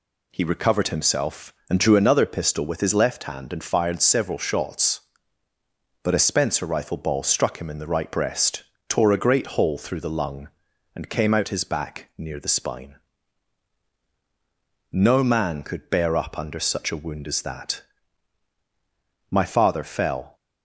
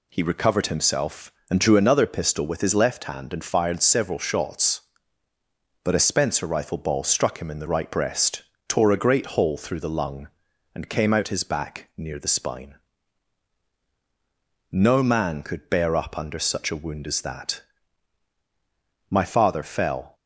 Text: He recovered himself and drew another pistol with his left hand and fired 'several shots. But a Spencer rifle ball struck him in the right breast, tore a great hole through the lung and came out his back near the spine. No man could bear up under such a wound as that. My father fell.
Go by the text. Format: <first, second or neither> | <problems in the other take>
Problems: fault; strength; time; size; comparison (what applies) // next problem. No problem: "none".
neither | none